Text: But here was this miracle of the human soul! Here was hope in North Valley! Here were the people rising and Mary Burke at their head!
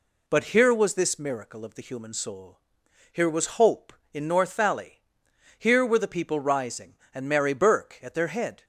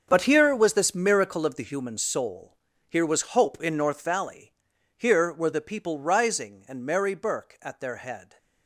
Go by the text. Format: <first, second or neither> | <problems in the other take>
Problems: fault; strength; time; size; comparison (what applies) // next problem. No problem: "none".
first | gets quieter; strong; throughout; 14 dB